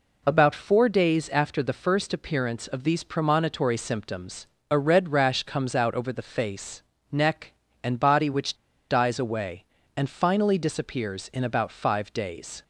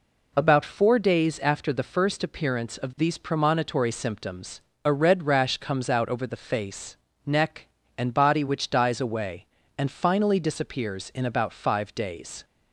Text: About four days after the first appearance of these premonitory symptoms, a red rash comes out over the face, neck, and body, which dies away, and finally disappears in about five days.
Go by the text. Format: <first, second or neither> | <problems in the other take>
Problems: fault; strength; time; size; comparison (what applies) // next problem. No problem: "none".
second | pauses between "which" and "dies"; slight; at 8.5 s; 0.35 s long